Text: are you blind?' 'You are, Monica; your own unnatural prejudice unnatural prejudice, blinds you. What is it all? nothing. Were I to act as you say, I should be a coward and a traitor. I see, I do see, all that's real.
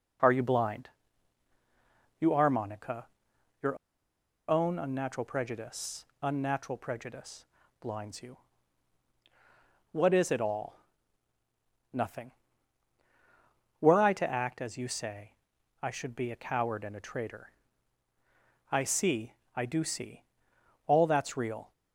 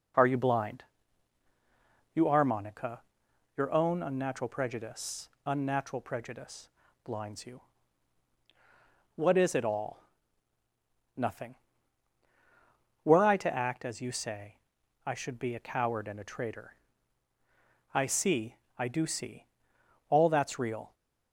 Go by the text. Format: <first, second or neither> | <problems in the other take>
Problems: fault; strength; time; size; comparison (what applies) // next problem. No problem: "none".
second | pauses between "your" and "own"; noticeable; at 3.7 s; 0.71 s long // pauses between "prejudice" and "unnatural"; slight; at 6.0 s; 0.20 s long; slight in the second